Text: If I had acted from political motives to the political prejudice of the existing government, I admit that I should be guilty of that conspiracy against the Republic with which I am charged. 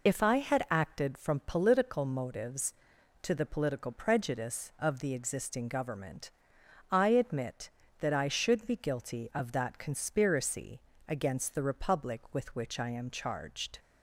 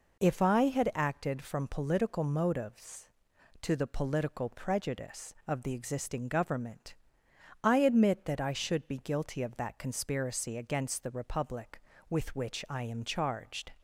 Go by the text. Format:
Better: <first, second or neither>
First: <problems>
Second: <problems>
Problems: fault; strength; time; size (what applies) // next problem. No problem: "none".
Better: second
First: loses the start of "If"; at 0.0 s; 40 ms // pauses between "conspiracy" and "against"; slight; at 10.8 s; 0.26 s long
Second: none